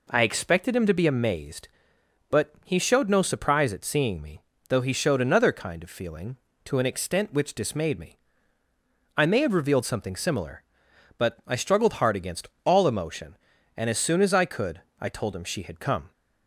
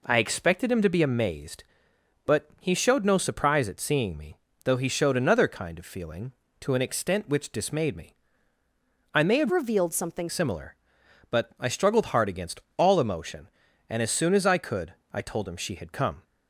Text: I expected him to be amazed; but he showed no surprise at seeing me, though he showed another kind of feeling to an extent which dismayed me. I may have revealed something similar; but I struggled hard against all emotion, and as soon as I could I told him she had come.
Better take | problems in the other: first | changes voice from "revealed" to "something"; from 9.5 to 10.2 s; 0.7 s long // pauses between "against" and "all"; slight; at 12.6 s; 0.16 s long; slight in the first // pauses between "could" and "I"; slight; at 14.9 s; 0.20 s long; slight in the first

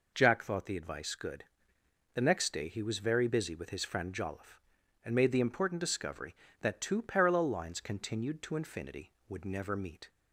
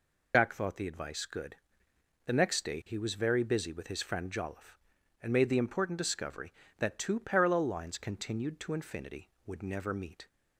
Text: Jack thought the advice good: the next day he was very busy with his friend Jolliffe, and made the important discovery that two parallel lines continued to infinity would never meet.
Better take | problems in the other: first | loses the start of "Jack"; at 0.3 s; 95 ms

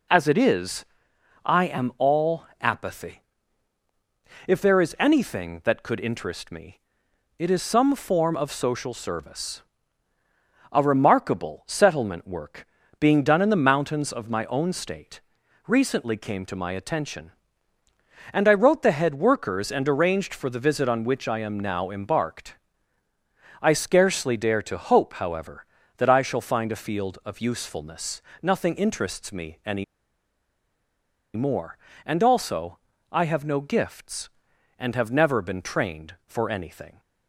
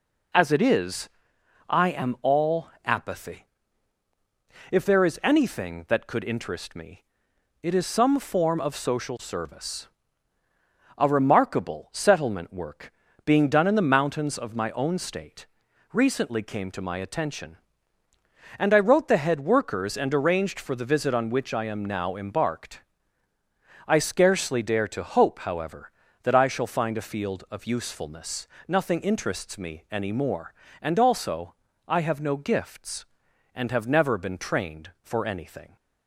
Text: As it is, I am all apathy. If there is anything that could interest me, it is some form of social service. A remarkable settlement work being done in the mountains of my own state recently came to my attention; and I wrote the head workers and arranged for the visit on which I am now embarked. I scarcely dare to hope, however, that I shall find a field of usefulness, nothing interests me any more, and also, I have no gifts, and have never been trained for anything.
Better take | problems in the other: second | pauses between "work" and "being"; slight; at 12.6 s; 0.34 s long; slight in the second // pauses between "state" and "recently"; noticeable; at 15.1 s; 0.46 s long; noticeable in the second // pauses between "any" and "more"; strong; at 29.8 s; 1.5 s long

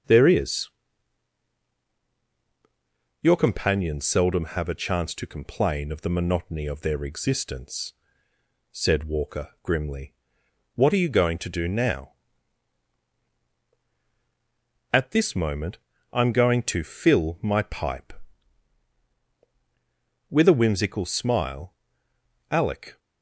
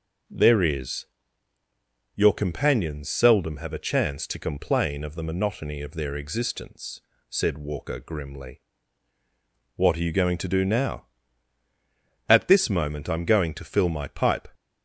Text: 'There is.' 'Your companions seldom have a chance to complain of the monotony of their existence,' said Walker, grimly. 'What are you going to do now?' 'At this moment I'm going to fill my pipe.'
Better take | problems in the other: second | starts louder than the rest; until 3.6 s; 6.5 dB // pauses between "moment" and "I'm"; slight; at 15.7 s; 0.34 s long // goes on to say "With a whimsical smile Alec"; strong; from 20.2 s on; 2.7 s long

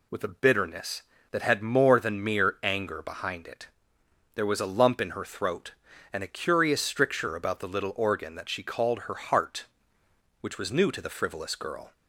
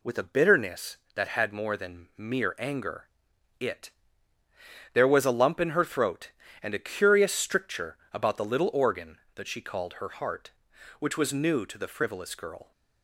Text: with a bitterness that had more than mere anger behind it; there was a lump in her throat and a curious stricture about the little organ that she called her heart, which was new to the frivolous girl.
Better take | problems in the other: first | skips "behind"; at 3.3 s // pauses between "stricture" and "about"; slight; at 7.9 s; 0.16 s long

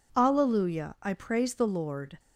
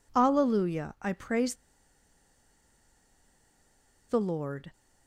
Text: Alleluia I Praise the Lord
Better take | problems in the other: first | pauses between "Praise" and "the"; strong; at 1.5 s; 2.5 s long

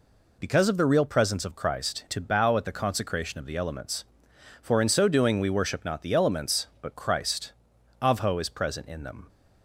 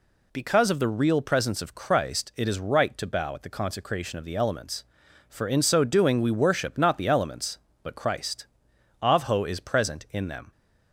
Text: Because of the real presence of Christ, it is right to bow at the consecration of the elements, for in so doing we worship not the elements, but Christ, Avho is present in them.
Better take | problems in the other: second | skips "it is right"; at 2.0 s

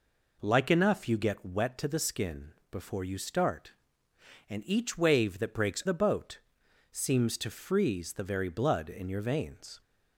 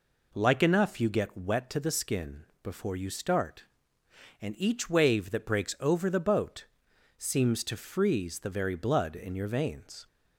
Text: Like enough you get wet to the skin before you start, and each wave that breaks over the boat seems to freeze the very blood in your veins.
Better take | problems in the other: second | pauses between "skin" and "before"; slight; at 2.5 s; 0.18 s long; slight in the second // skips "over"; at 5.8 s // pauses between "boat" and "seems"; noticeable; at 6.4 s; 0.52 s long; noticeable in the second

